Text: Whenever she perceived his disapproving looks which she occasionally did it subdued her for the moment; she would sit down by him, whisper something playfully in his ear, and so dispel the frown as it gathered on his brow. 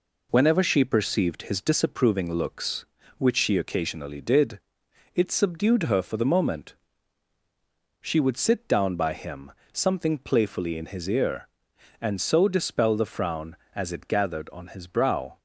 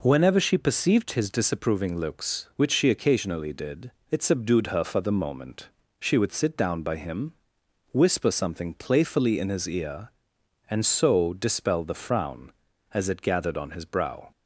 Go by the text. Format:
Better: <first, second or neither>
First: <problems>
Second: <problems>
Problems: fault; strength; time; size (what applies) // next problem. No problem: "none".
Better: second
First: pauses between "did" and "it"; noticeable; at 4.6 s; 0.52 s long // skips "whisper"; at 9.6 s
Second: pauses between "did" and "it"; slight; at 3.9 s; 0.18 s long